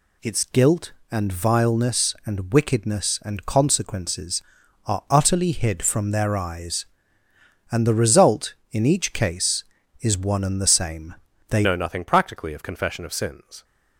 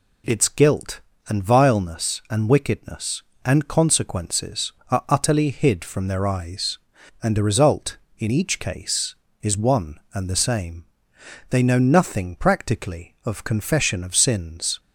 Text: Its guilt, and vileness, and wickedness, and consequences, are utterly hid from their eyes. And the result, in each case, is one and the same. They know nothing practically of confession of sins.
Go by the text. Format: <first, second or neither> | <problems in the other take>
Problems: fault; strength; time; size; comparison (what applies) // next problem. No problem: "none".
second | changes voice at "know"; from 11.6 s on; 2.0 s long